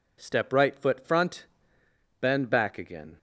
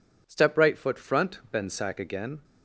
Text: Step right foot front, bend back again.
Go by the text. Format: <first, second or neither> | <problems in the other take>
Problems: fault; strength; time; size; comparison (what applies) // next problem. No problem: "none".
first | says "sack" for "back"; at 1.7 s